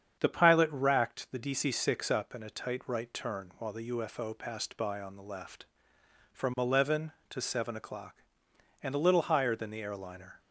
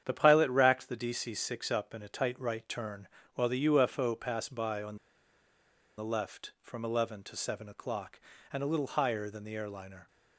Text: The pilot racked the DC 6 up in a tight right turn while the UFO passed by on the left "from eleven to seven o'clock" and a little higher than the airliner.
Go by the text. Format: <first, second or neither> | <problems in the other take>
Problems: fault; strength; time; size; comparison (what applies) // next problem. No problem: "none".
first | starts louder than the rest; strong; until 1.0 s; 9 dB; strong in the first // pauses between "turn" and "while"; slight; at 3.0 s; 0.28 s long // pauses between "on" and "the"; at 4.9 s; 1.0 s long